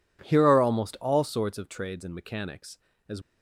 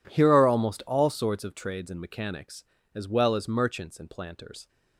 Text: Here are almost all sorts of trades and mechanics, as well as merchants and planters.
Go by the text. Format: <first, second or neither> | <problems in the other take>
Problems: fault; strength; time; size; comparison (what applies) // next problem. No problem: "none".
second | stops before "well as merchants and planters"; at 3.2 s